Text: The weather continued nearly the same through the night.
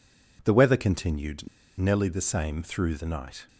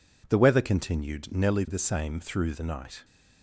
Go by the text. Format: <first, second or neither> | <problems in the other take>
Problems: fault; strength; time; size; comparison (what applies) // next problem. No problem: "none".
second | pauses between "continued" and "nearly"; slight; at 1.4 s; 0.30 s long